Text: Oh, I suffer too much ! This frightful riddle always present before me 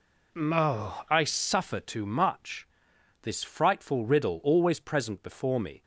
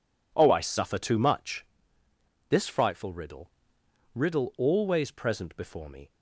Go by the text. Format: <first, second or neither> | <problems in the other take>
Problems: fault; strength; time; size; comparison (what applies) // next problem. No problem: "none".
first | says "riddle" twice; at 4.1 s